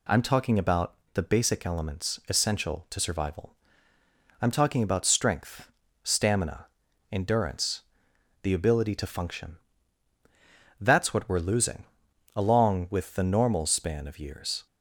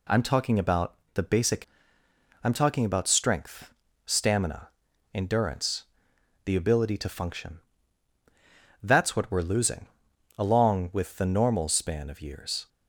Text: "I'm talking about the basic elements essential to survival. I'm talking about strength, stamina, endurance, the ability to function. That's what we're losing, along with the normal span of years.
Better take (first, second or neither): first